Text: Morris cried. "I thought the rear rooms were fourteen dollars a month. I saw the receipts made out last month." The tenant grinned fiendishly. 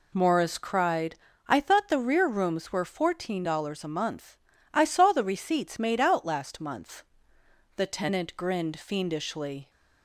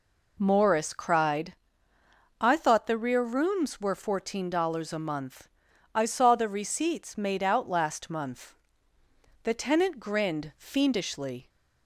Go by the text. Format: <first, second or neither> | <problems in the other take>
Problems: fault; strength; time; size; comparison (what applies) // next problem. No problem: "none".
neither | none